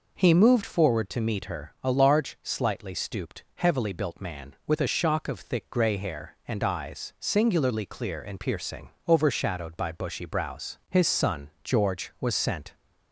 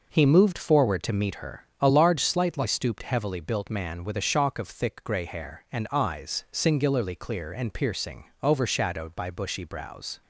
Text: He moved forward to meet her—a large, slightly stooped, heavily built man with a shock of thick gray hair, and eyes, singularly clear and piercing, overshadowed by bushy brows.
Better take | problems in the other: second | goes on to say "His son George was sent"; strong; from 10.8 s on; 1.8 s long

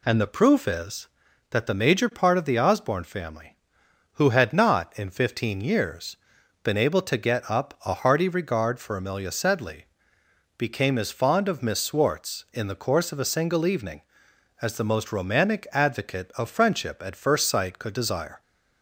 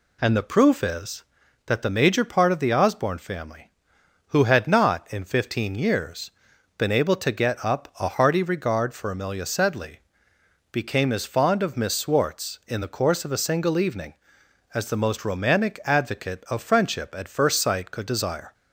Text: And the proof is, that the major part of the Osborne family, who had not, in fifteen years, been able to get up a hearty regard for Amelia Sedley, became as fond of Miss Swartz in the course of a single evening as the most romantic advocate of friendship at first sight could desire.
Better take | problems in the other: neither | none

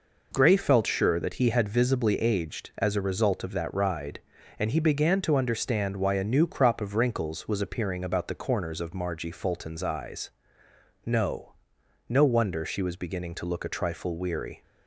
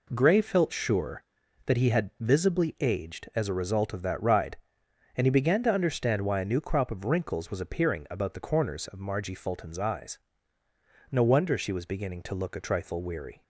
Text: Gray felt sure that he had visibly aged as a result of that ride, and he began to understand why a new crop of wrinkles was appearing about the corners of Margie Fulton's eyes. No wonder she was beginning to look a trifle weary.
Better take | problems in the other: second | says "No" twice; at 12.0 s

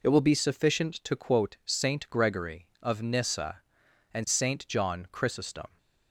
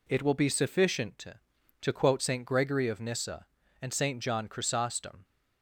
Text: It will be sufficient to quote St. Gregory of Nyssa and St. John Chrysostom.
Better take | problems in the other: first | says "to" twice; at 1.8 s

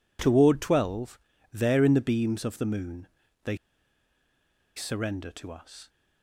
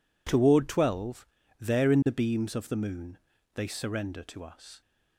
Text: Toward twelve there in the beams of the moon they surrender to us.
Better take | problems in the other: second | pauses between "twelve" and "there"; slight; at 1.1 s; 0.32 s long; slight in the second // pauses between "moon" and "they"; at 3.0 s; 0.38 s long; also in the second // pauses between "they" and "surrender"; at 3.5 s; 1.1 s long

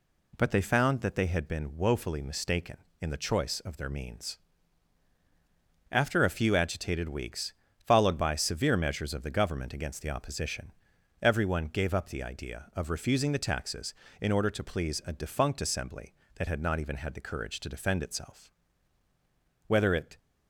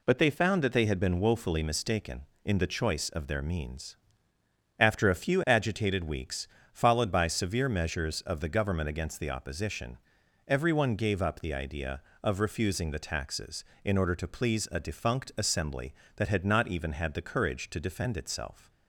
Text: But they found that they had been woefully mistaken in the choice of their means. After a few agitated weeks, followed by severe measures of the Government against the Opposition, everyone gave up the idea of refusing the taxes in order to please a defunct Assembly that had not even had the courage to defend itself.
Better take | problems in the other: second | goes on to say "Whether it"; from 19.6 s on; 0.50 s long

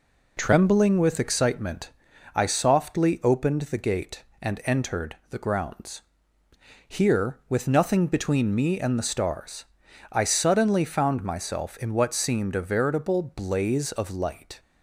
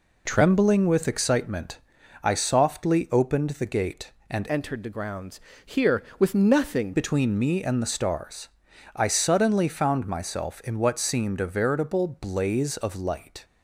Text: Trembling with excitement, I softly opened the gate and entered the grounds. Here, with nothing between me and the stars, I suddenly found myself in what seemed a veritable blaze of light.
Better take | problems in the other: first | changes voice from "entered" to "nothing"; from 4.4 to 6.9 s; 2.5 s long

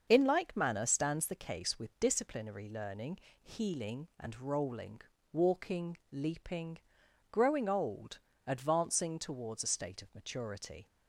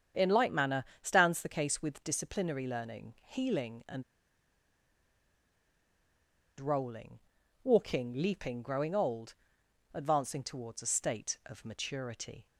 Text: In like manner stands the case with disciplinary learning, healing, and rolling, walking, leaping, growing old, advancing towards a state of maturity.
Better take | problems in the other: first | starts louder than the rest; strong; until 1.3 s; 8 dB; also in the first // pauses between "manner" and "stands"; slight; at 0.8 s; 0.16 s long // pauses between "and" and "rolling"; strong; at 4.0 s; 2.5 s long

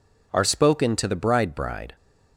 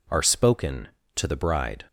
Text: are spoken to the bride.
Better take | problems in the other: second | says "bride" twice; at 1.5 s

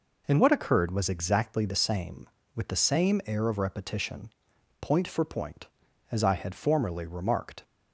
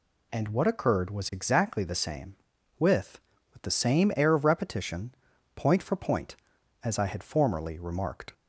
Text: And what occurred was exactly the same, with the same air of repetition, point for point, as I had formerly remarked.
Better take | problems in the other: first | says "with" twice; at 3.5 s

